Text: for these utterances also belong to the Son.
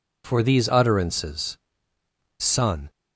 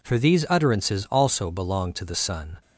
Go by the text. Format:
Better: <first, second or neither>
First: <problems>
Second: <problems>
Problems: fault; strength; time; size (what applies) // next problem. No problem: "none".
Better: second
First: skips "also belong to the"; at 1.9 s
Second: none